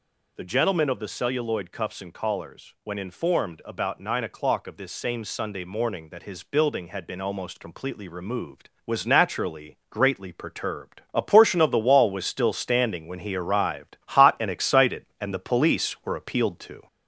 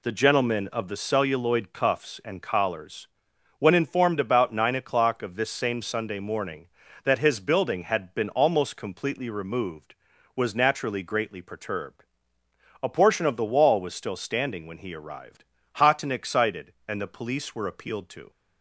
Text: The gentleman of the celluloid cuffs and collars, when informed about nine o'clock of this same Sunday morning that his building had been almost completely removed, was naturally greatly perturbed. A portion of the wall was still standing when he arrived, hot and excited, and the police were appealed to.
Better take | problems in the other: second | gets louder; slight; throughout; 3 dB

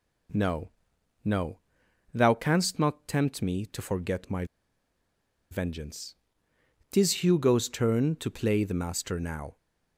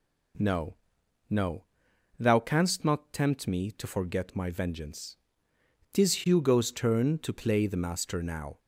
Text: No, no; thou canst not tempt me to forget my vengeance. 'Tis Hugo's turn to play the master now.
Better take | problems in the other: second | pauses between "my" and "vengeance"; at 4.4 s; 1.0 s long

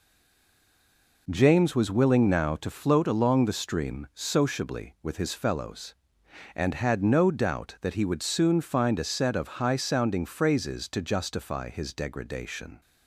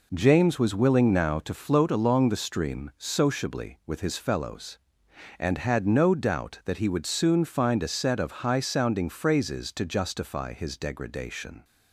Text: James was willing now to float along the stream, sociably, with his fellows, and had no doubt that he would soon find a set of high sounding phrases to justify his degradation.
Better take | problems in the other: second | stays silent before the first word; noticeable; until 1.2 s; 1.2 s long

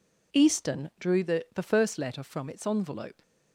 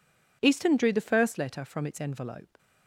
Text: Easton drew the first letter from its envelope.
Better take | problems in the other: second | says "the" twice; at 1.5 s

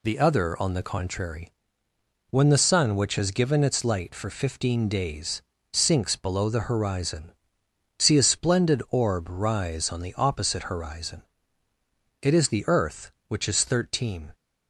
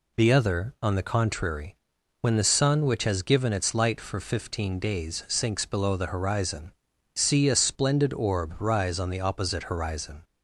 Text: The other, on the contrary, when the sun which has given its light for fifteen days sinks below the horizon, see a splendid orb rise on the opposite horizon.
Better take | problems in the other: second | pauses between "days" and "sinks"; slight; at 5.4 s; 0.32 s long // goes on to say "It is the earth which is thirteen"; strong; from 12.2 s on; 2.1 s long

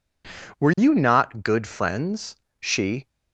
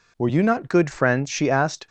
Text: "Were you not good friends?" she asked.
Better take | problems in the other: second | stops before "asked"; at 3.0 s

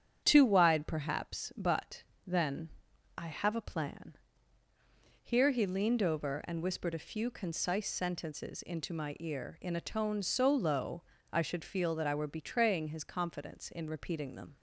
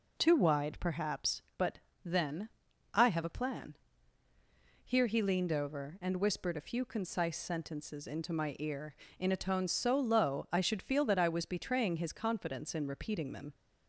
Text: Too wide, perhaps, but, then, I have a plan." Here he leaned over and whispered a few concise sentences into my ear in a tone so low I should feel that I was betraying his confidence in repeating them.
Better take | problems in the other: second | starts louder than the rest; strong; until 1.2 s; 9 dB // pauses between "low" and "I"; slight; at 11.0 s; 0.30 s long // says "were" for "was"; at 12.1 s

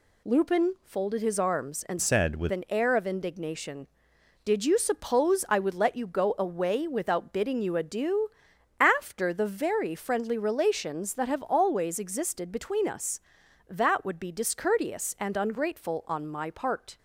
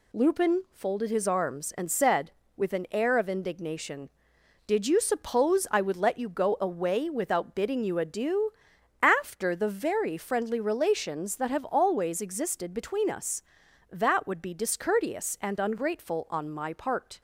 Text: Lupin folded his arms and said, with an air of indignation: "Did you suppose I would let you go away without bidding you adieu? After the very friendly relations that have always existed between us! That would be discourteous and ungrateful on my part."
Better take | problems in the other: second | changes voice from "said" to "with"; from 2.0 to 2.5 s; 0.5 s long

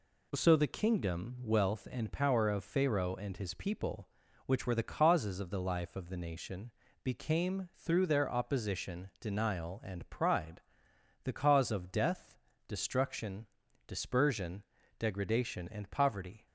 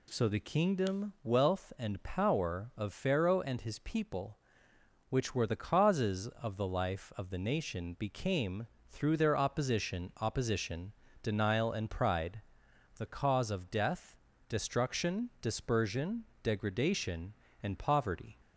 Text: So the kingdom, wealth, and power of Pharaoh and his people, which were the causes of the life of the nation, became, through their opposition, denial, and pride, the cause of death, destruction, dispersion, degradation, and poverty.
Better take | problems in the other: first | says "opposition" twice; at 10.1 s

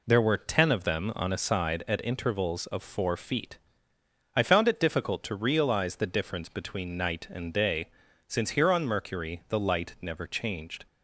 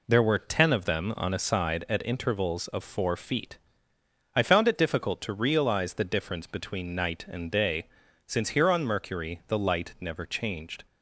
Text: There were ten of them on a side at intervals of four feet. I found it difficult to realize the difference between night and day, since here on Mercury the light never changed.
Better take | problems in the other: neither | none

